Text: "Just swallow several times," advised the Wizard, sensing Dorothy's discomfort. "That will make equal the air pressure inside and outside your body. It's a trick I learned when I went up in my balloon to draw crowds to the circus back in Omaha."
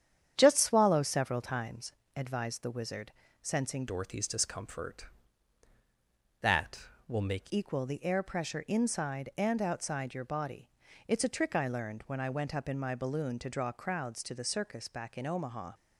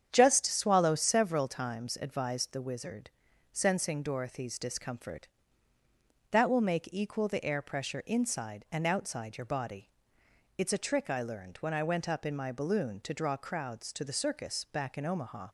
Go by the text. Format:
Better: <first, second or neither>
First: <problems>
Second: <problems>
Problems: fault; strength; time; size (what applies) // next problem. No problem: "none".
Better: second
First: starts louder than the rest; strong; until 1.3 s; 9 dB // changes voice from "Dorothy's" to "make"; from 3.8 to 7.5 s; 3.7 s long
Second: starts louder than the rest; strong; until 1.1 s; 8.5 dB